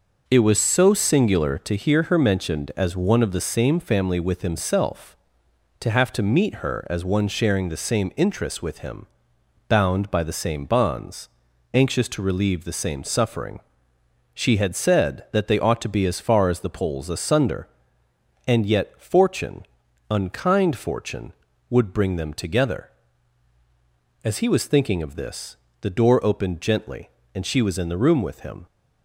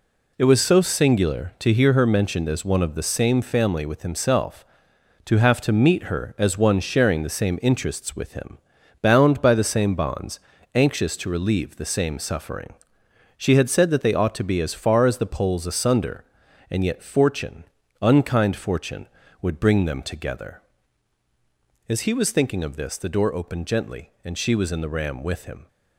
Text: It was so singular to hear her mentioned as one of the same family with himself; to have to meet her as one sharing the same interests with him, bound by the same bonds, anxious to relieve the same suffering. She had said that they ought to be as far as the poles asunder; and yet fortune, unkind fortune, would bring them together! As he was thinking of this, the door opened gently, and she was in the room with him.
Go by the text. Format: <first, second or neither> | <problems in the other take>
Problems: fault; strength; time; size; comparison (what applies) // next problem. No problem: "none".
first | says "ram" for "room"; at 24.8 s